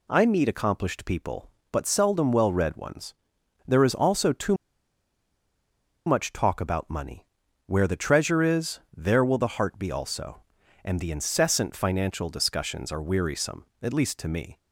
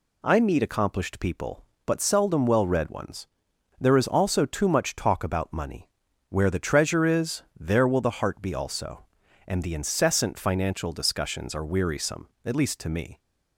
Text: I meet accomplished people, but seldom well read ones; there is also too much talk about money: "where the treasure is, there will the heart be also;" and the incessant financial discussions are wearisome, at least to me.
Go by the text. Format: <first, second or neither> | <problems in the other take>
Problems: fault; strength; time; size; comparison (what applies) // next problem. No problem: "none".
second | pauses between "too" and "much"; strong; at 4.5 s; 1.5 s long